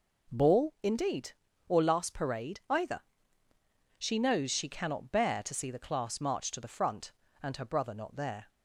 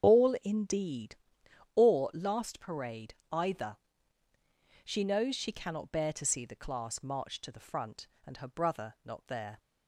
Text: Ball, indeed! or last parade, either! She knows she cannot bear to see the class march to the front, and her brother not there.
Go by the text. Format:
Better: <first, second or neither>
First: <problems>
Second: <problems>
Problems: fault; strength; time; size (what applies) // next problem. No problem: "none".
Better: first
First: none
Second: loses the start of "Ball"; at 0.0 s; 40 ms // starts louder than the rest; strong; until 1.1 s; 8 dB